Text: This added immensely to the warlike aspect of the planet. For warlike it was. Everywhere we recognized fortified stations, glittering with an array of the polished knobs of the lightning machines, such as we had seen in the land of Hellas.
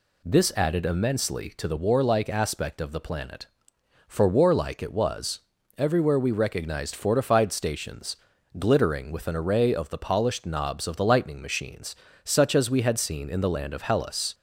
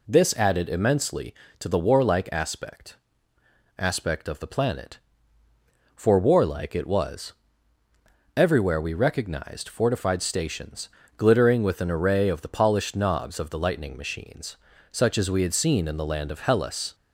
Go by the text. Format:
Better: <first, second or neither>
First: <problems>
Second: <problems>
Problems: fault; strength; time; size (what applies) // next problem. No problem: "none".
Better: first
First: none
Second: says "aspect" twice; at 3.7 s